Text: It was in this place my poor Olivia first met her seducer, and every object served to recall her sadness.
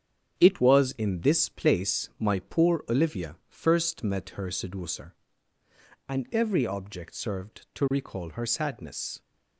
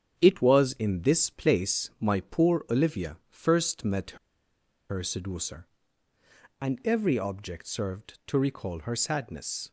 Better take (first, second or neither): first